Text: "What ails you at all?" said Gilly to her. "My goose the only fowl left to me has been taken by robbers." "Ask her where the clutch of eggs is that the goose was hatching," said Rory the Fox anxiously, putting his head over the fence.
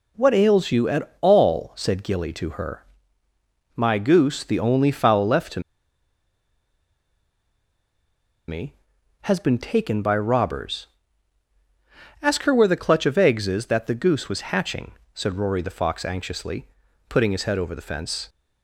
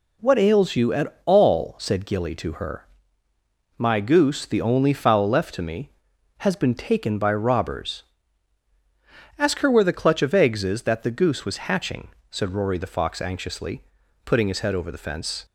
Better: second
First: pauses between "to" and "me"; strong; at 5.6 s; 2.8 s long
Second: none

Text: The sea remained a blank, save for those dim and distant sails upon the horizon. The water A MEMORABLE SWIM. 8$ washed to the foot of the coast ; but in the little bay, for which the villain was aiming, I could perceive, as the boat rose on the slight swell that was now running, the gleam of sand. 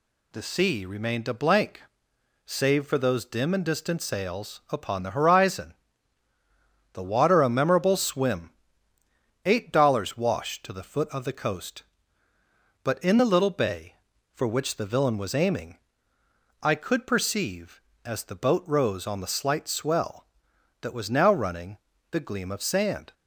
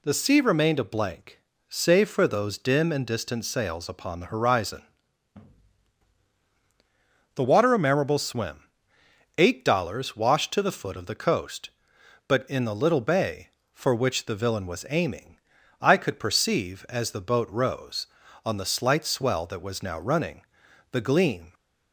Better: first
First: none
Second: stops before "of sand"; at 21.5 s

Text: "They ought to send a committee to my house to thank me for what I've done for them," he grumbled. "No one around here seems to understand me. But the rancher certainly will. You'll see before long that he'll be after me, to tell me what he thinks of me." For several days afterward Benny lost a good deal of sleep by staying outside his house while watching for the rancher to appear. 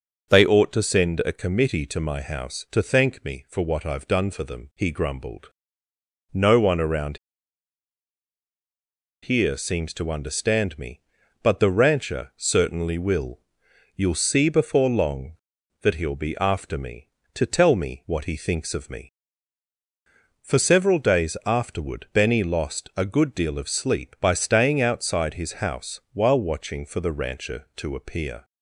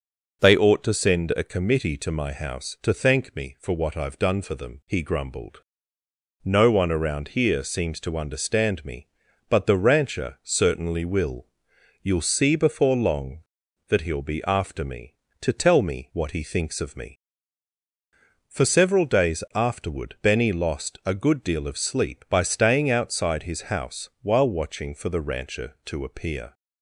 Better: second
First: starts louder than the rest; noticeable; until 1.3 s; 6 dB // pauses between "around" and "here"; strong; at 7.1 s; 2.0 s long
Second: starts louder than the rest; noticeable; until 1.4 s; 6 dB

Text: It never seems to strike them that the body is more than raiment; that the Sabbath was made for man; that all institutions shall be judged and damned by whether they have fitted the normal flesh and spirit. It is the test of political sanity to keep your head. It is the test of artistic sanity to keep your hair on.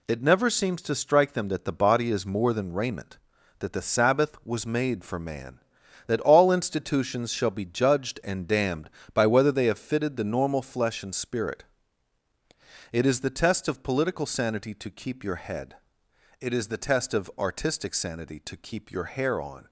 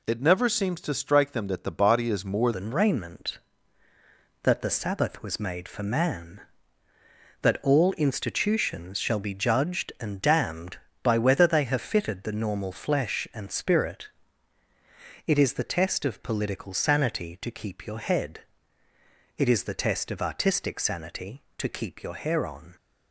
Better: first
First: none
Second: changes voice at "than"; from 2.5 s on; 20.2 s long

